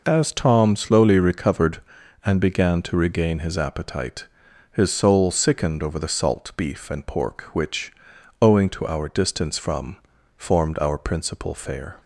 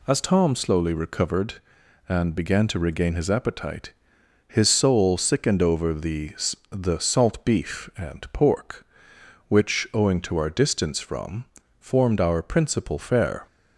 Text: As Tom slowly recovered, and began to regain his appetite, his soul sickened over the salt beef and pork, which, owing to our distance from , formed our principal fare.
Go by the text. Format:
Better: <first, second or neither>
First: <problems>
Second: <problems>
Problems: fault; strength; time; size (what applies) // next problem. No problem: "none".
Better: first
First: none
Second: says "the" twice; at 6.6 s